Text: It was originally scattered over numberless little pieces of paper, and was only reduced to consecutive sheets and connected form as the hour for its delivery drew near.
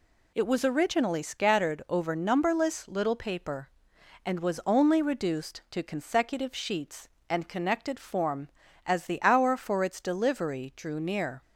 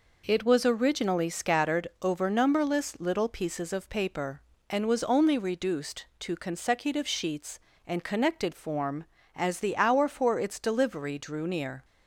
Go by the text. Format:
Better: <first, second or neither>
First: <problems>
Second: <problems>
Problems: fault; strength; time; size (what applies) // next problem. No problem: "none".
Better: second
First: skips "pieces of"; at 3.1 s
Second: none